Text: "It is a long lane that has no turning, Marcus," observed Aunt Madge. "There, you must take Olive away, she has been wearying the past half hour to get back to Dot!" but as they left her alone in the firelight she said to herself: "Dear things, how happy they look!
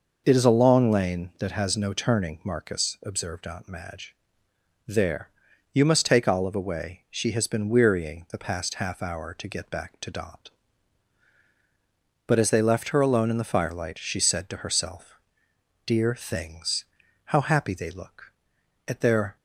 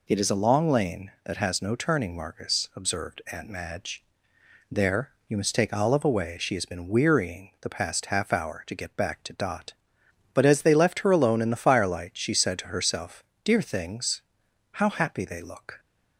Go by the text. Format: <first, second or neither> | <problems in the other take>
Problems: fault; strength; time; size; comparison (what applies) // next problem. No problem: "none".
second | goes on to say "at their"; from 18.8 s on; 0.50 s long